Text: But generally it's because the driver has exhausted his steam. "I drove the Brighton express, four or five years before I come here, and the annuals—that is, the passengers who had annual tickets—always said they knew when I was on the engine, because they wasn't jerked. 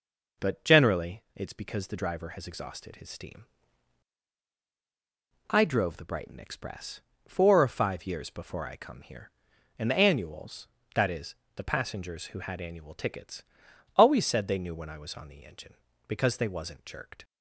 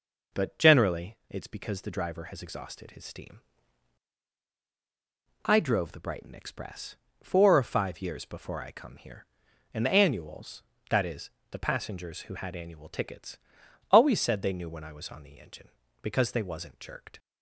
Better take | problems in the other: neither | none

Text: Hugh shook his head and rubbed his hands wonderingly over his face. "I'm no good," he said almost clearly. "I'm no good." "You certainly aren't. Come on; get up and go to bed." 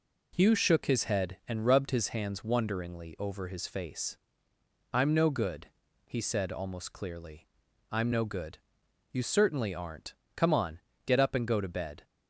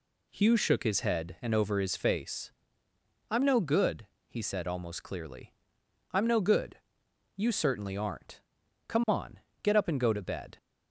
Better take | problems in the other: first | skips "rubbed his hands wonderingly"; at 1.5 s

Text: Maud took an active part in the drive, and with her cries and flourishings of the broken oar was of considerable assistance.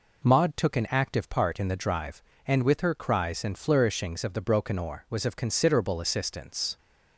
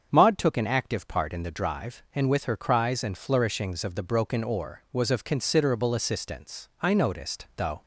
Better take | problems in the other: first | starts louder than the rest; until 1.1 s; 7 dB // goes on to say "I noticed though"; noticeable; from 6.7 s on; 1.0 s long

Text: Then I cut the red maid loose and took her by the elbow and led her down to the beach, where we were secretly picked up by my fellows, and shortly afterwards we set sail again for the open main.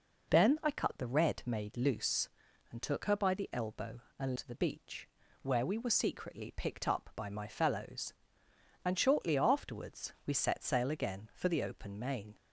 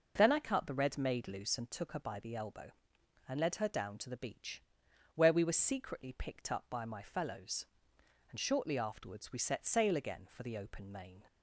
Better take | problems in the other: second | skips "led her down"; at 4.3 s

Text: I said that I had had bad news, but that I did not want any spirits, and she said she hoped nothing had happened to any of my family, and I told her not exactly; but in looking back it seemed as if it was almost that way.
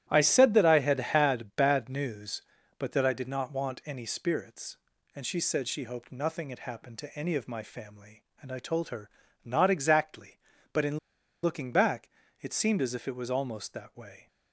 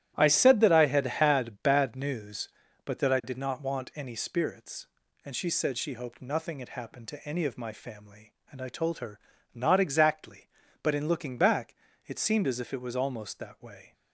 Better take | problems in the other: second | starts louder than the rest; strong; until 1.0 s; 12.5 dB; strong in the second // pauses between "her" and "not"; slight; at 9.0 s; 0.34 s long; slight in the second // pauses between "in" and "looking"; noticeable; at 10.9 s; 0.46 s long // pauses between "back" and "it"; slight; at 12.0 s; 0.32 s long; slight in the second

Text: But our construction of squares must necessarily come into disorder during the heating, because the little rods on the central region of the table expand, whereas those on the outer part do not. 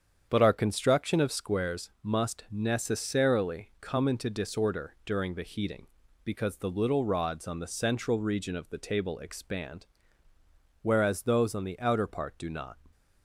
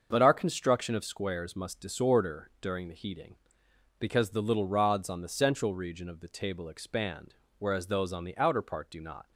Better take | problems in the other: first | starts louder than the rest; until 1.1 s; 6.5 dB; strong in the first // skips "necessarily come into"; at 1.7 s

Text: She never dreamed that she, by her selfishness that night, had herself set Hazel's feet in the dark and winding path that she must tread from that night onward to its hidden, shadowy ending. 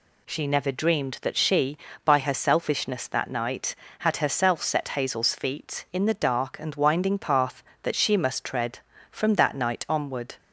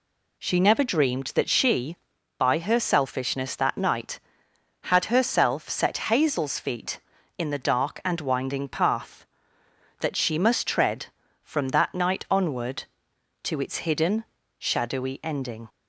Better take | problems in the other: second | stops before "to its hidden shadowy ending"; at 10.3 s

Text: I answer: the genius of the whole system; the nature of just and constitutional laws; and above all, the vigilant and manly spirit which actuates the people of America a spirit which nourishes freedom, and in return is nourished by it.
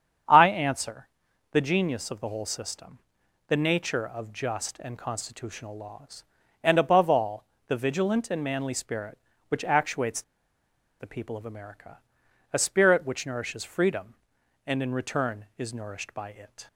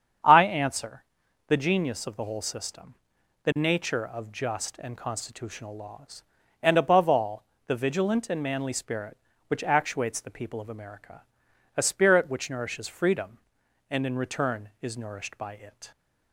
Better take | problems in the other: second | starts louder than the rest; strong; until 1.7 s; 7.5 dB; strong in the second // pauses between "actuates" and "the"; noticeable; at 10.2 s; 0.77 s long // pauses between "America" and "a"; noticeable; at 11.9 s; 0.52 s long; noticeable in the second

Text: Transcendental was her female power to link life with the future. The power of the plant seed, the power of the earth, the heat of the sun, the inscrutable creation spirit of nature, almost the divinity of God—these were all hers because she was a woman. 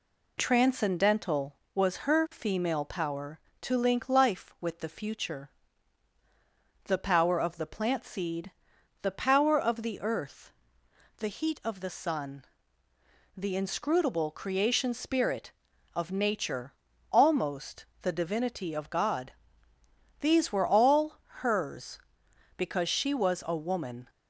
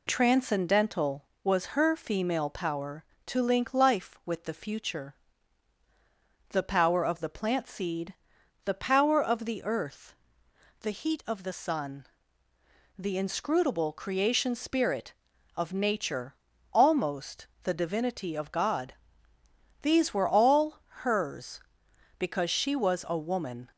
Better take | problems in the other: neither | pauses between "almost" and "the"; slight; the same in both // pauses between "all" and "hers"; slight; the same in both

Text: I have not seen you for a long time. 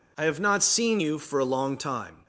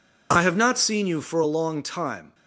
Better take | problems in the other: neither | none

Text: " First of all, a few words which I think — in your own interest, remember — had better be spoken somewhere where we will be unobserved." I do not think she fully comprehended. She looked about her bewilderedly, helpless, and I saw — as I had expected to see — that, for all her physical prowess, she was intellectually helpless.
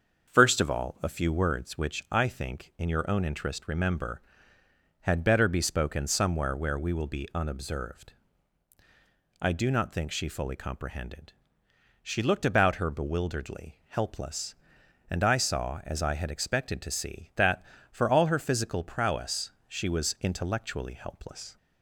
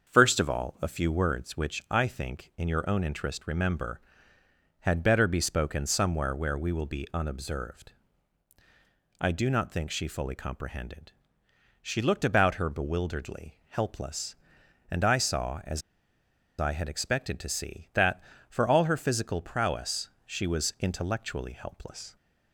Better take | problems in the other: first | starts louder than the rest; until 1.1 s; 6.5 dB; also in the first // pauses between "as" and "I"; noticeable; at 15.8 s; 0.78 s long

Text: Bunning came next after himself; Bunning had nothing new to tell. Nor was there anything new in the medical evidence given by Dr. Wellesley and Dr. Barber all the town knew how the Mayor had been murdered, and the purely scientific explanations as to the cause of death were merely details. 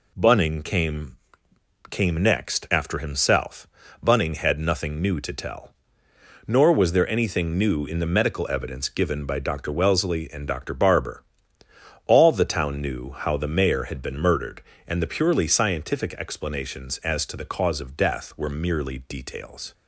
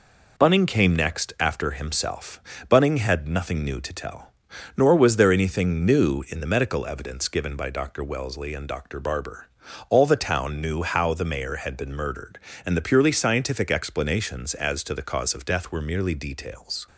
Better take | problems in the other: second | says "came" twice; at 1.8 s // pauses between "Barber" and "all"; noticeable; at 11.2 s; 0.82 s long; also in the second

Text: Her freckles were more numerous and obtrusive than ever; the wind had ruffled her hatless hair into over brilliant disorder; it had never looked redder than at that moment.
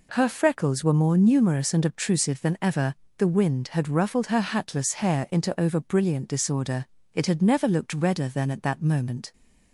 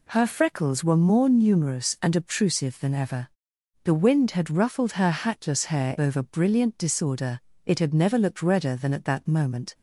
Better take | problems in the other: first | skips "into"; at 5.9 s

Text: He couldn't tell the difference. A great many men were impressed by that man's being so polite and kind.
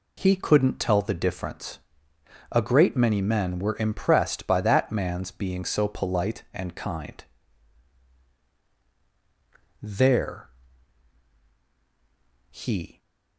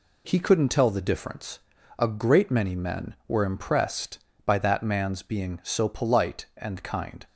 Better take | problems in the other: second | goes on to say "There he"; strong; from 9.8 s on; 3.1 s long

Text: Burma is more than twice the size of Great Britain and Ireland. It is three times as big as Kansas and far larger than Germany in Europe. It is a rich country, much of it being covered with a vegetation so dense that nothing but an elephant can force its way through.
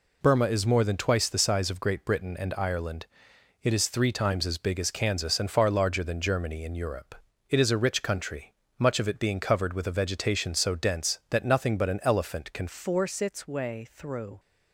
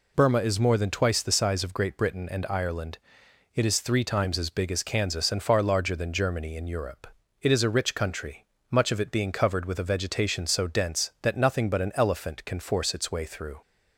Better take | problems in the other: second | changes voice at "force"; from 12.6 s on; 1.7 s long

